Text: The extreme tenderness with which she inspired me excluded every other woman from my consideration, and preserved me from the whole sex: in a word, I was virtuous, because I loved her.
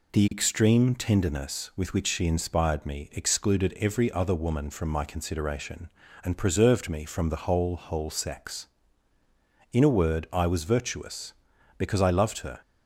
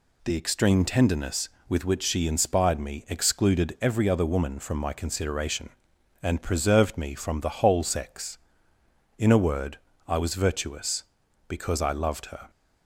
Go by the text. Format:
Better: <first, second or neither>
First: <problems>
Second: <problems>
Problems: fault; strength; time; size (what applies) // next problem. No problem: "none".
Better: second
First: says "whole" twice; at 7.7 s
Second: none